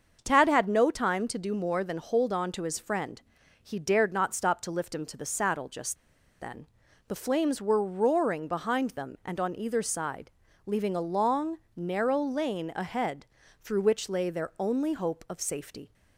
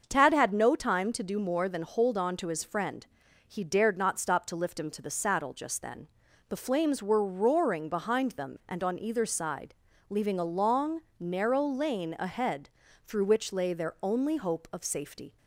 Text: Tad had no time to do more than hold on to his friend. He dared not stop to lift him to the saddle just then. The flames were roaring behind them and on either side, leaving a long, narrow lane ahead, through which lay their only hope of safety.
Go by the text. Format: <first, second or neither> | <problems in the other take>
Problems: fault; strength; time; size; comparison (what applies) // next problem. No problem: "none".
second | starts louder than the rest; until 1.2 s; 6.5 dB; also in the second // pauses between "just" and "then"; at 5.9 s; 0.44 s long